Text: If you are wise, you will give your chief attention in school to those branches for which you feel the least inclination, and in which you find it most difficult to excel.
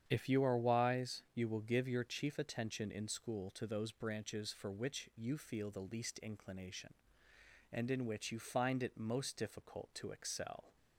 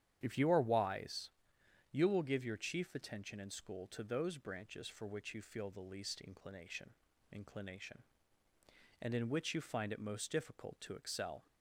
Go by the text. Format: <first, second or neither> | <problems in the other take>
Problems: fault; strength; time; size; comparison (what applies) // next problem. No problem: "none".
first | starts louder than the rest; strong; until 1.2 s; 10 dB; strong in the first // says "inclination" twice; at 7.3 s